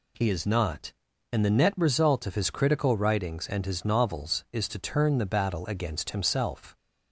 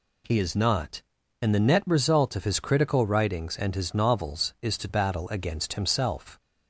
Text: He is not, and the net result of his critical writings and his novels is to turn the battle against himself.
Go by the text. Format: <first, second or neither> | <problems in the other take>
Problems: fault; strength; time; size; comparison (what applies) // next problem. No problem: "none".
first | skips "turn the"; at 4.8 s